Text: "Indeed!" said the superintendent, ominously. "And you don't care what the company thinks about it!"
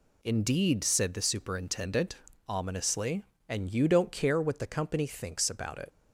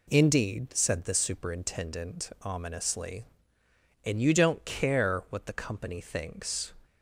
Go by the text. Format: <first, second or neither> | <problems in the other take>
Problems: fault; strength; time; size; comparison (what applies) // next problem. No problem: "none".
first | stops before "about it"; at 6.8 s